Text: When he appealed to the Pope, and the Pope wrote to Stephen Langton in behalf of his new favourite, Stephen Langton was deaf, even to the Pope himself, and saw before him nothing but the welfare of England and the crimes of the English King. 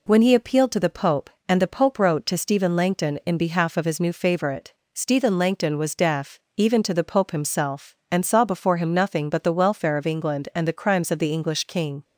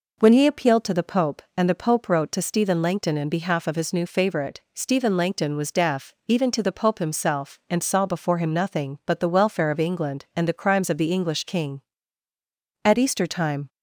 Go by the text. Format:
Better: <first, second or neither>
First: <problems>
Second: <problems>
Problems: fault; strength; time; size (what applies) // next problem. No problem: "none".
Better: first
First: none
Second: goes on to say "At Easter time"; noticeable; from 12.8 s on; 0.86 s long